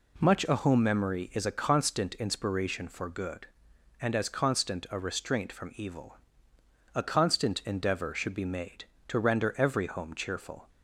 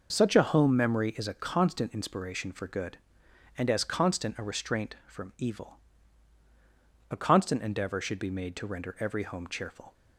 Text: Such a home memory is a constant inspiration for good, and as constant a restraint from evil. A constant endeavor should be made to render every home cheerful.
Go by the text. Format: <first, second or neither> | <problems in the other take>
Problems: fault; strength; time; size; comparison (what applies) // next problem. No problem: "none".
second | says "Much" for "Such"; at 0.1 s